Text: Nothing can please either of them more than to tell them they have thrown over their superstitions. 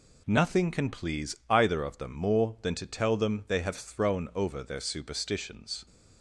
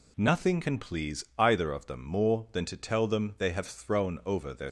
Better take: first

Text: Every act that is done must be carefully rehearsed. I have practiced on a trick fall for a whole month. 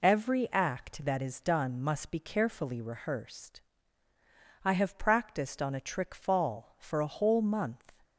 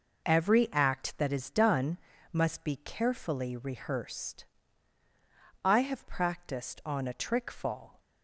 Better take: first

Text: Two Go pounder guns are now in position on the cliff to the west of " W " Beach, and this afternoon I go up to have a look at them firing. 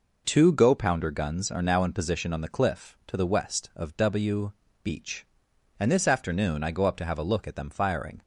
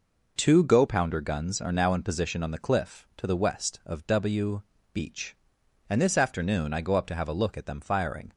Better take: neither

